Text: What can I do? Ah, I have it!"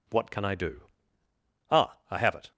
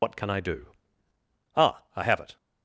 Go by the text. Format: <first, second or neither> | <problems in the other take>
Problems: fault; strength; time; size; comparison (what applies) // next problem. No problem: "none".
first | loses the start of "What"; at 0.0 s; 80 ms